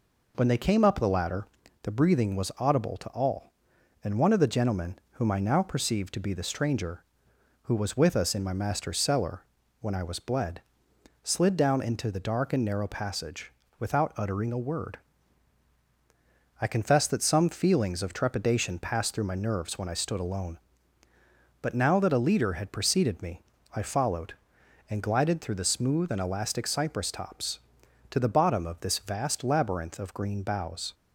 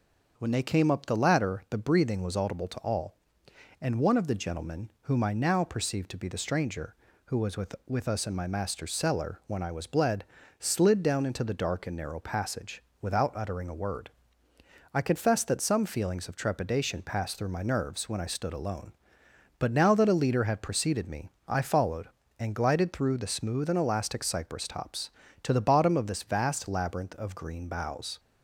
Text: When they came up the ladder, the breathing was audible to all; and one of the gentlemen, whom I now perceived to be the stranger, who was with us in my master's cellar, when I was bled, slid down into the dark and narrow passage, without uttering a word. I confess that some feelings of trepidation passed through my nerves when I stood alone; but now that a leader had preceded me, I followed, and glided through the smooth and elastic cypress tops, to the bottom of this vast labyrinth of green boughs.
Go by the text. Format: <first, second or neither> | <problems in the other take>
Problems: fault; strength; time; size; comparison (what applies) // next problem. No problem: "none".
first | starts louder than the rest; until 1.3 s; 6.5 dB // says "with" twice; at 7.8 s